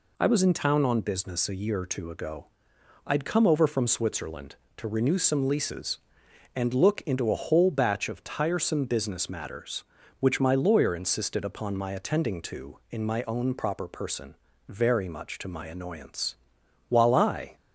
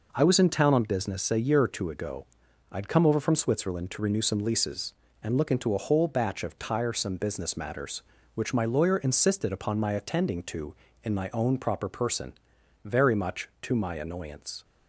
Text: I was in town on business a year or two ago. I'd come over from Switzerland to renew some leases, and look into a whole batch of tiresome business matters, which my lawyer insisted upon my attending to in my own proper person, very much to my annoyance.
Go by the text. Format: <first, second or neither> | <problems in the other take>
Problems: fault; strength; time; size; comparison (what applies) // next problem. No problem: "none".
second | goes on to say "While I"; noticeable; from 16.8 s on; 0.68 s long